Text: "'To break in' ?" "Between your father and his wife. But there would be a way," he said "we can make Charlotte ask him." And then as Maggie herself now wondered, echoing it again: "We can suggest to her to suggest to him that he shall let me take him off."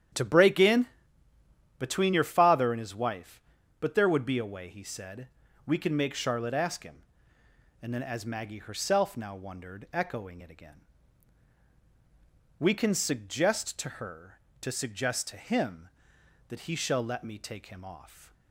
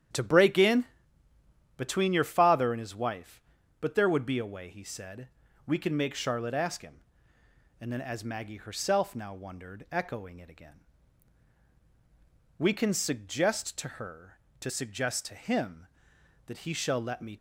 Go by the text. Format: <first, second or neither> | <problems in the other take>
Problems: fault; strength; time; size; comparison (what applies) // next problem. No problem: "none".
first | starts louder than the rest; strong; until 1.5 s; 8 dB; strong in the first // pauses between "said" and "we"; slight; at 5.2 s; 0.36 s long; slight in the first // stops before "take him off"; at 17.3 s